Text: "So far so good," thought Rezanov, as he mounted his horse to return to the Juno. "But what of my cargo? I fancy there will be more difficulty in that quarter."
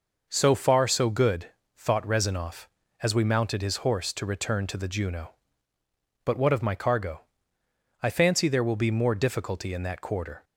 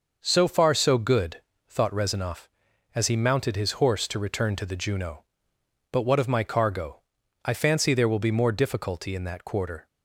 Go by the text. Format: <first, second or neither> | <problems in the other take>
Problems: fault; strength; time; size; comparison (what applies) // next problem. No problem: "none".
second | says "we" for "he"; at 3.1 s